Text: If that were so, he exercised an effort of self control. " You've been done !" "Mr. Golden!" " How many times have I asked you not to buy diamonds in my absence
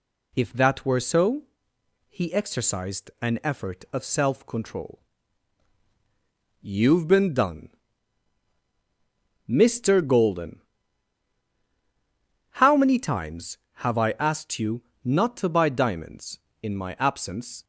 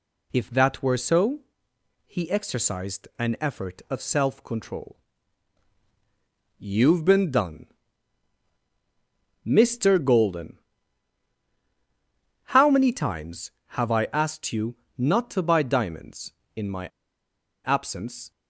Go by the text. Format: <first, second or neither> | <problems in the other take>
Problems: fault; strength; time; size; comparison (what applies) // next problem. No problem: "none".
first | pauses between "you" and "not"; slight; at 14.7 s; 0.20 s long; slight in the first // pauses between "my" and "absence"; noticeable; at 16.8 s; 0.79 s long